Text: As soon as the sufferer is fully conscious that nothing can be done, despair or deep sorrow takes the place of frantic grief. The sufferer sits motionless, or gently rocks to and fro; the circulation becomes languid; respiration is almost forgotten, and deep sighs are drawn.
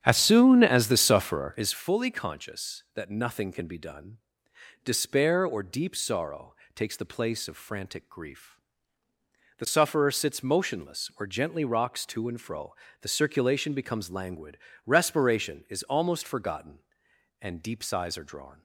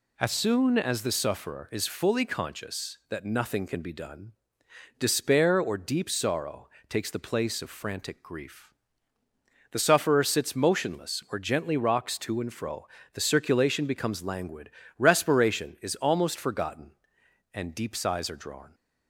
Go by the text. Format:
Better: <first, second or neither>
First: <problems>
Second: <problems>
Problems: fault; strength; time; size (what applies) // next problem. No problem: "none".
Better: second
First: starts louder than the rest; strong; until 1.8 s; 9 dB // pauses between "sorrow" and "takes"; slight; at 6.5 s; 0.18 s long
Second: pauses between "sorrow" and "takes"; slight; at 6.6 s; 0.18 s long